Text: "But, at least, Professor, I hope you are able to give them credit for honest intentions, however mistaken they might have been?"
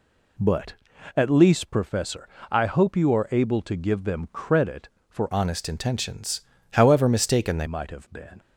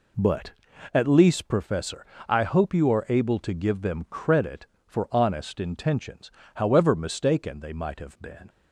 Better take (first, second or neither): second